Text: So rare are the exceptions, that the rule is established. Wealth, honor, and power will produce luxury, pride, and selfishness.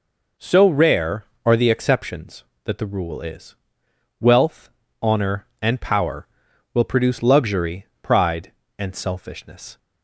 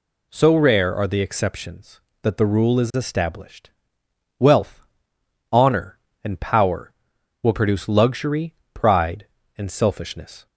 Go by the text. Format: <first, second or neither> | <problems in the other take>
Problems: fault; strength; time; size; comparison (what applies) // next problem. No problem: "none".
second | skips "established"; at 3.8 s